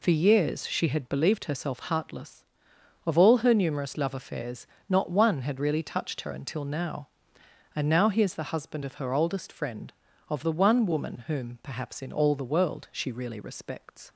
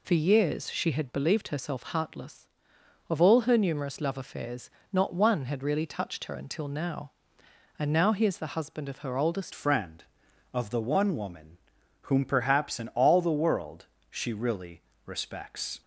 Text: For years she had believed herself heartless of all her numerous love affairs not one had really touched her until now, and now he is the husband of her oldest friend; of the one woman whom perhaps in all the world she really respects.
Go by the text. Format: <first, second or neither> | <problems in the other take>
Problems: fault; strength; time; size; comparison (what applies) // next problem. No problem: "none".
first | pauses between "affairs" and "not"; slight; at 4.6 s; 0.22 s long; slight in the first // changes voice at "friend"; from 9.5 s on; 6.3 s long // pauses between "woman" and "whom"; noticeable; at 11.5 s; 0.46 s long // pauses between "world" and "she"; slight; at 13.8 s; 0.26 s long // pauses between "really" and "respects"; slight; at 14.8 s; 0.22 s long